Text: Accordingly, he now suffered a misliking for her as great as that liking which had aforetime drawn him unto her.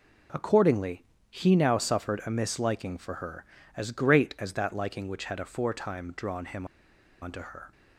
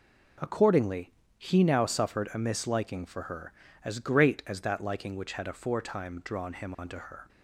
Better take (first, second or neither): second